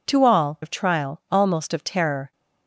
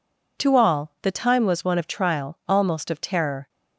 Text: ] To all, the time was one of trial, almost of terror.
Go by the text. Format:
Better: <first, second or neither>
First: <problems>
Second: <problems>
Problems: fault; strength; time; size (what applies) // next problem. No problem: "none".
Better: second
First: skips "the time was one"; at 0.6 s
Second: none